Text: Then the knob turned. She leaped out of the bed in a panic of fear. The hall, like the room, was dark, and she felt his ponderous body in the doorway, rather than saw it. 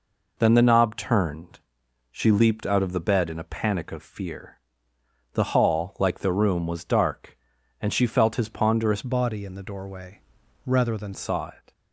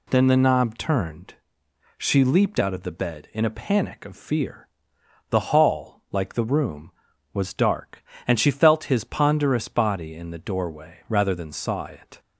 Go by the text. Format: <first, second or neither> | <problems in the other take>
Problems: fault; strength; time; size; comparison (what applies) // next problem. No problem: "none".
second | changes voice from "body" to "than"; from 9.0 to 11.1 s; 2.1 s long